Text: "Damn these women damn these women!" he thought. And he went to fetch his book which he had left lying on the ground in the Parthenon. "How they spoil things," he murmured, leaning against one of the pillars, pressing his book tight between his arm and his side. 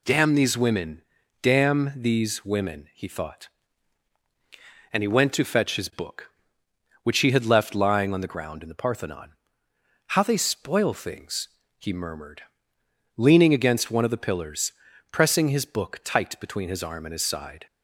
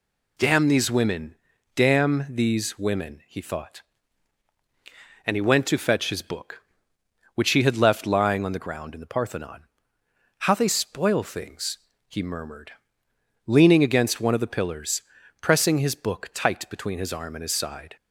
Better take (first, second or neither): neither